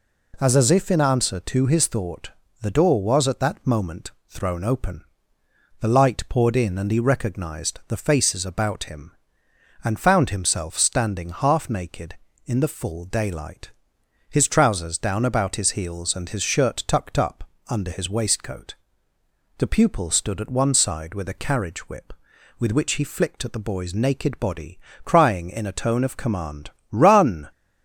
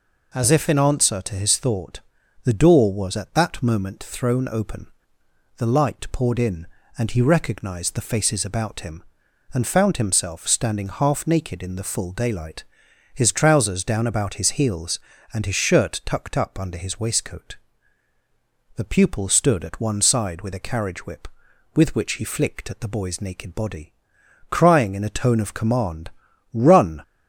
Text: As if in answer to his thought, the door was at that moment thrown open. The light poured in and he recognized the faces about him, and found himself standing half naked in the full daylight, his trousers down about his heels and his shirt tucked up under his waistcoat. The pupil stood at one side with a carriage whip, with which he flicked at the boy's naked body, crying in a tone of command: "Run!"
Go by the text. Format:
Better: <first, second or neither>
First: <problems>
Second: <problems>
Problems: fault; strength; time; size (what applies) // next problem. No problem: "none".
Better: second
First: says "As" twice; at 0.5 s // pauses between "moment" and "thrown"; slight; at 4.1 s; 0.16 s long // pauses between "up" and "under"; slight; at 17.4 s; 0.24 s long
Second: none